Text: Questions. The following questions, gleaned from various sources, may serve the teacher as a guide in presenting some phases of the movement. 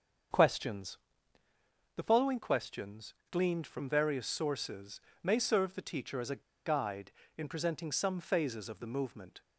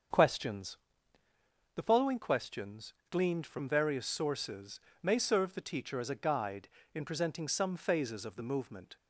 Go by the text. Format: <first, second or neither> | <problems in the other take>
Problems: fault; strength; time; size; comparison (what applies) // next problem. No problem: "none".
second | starts louder than the rest; until 2.3 s; 7 dB; also in the second // pauses between "a" and "guide"; slight; at 6.4 s; 0.22 s long